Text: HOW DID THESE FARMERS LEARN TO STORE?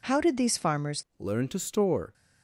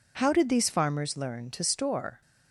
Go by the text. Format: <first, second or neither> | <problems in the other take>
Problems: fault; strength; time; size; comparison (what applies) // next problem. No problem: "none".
second | changes voice at "LEARN"; from 1.1 s on; 1.0 s long